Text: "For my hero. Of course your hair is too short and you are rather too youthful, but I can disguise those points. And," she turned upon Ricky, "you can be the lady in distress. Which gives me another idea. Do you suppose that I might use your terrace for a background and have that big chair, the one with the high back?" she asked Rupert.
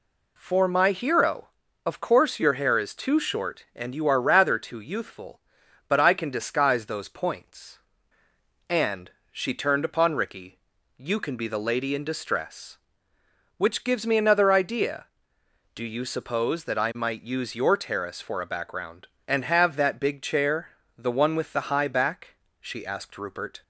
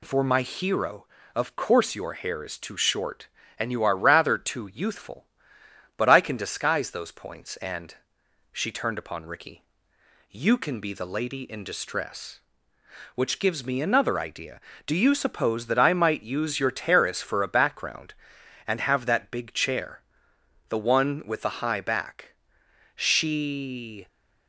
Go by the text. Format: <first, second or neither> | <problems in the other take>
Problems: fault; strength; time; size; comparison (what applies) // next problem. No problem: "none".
first | stops before "asked Rupert"; at 24.0 s